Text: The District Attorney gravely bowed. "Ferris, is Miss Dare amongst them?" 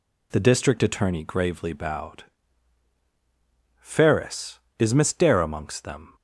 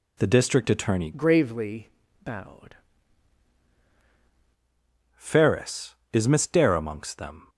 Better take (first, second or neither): first